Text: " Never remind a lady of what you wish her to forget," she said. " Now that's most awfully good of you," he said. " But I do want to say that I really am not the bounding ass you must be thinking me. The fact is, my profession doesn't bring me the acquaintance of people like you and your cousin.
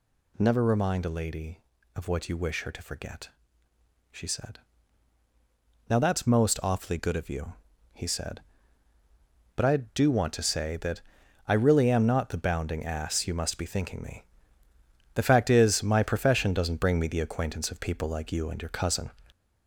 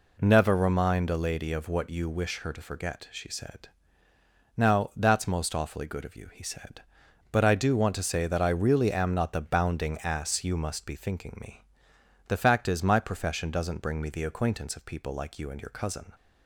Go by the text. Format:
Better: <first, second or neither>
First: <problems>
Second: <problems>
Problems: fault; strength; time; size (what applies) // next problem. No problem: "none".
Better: second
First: gets louder; strong; throughout; 9 dB // pauses between "that" and "I"; noticeable; at 11.0 s; 0.46 s long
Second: none